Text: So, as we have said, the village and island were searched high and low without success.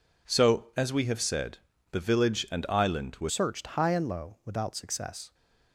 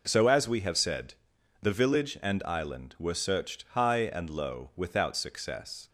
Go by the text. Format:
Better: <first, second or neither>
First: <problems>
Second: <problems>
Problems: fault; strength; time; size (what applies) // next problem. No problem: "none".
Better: second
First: changes voice at "searched"; from 3.2 s on; 2.1 s long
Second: none